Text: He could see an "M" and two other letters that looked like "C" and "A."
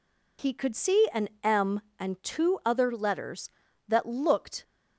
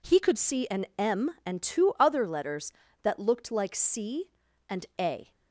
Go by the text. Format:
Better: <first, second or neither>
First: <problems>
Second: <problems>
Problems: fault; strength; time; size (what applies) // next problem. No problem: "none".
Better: second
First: pauses between "an" and "M"; slight; at 1.2 s; 0.16 s long // stops before "like C and A"; at 4.6 s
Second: none